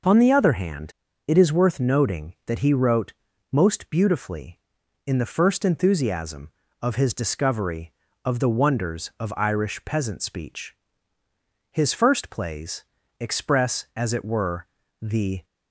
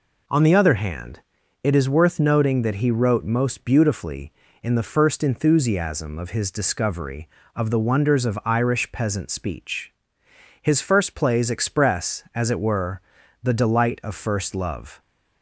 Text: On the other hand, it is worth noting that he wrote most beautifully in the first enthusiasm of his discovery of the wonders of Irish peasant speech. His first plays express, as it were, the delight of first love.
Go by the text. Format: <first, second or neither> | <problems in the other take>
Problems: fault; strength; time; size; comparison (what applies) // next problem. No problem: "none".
second | pauses between "wrote" and "most"; slight; at 3.1 s; 0.36 s long // pauses between "plays" and "express"; slight; at 12.8 s; 0.34 s long // stops before "delight of first love"; at 15.4 s